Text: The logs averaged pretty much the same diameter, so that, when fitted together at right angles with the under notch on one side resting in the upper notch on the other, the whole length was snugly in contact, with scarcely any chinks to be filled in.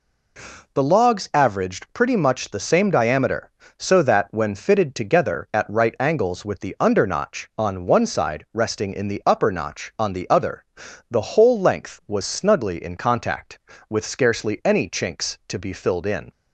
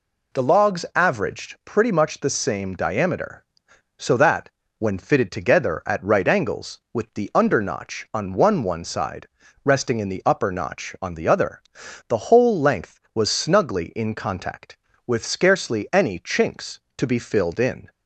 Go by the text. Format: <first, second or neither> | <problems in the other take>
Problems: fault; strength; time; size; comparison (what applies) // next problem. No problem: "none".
first | says "one" twice; at 8.6 s // pauses between "side" and "resting"; at 9.2 s; 0.38 s long